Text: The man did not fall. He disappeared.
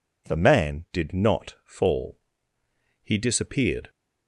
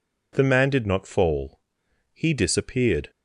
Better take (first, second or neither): neither